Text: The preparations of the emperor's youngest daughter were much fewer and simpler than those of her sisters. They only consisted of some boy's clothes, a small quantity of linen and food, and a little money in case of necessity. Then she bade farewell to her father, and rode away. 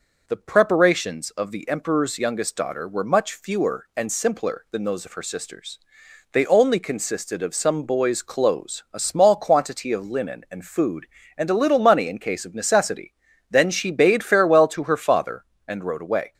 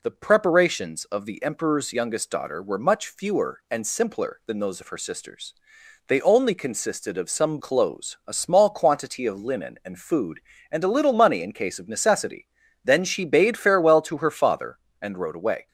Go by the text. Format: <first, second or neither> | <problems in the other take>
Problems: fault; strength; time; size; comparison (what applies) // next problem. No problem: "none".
first | skips "boy's"; at 7.5 s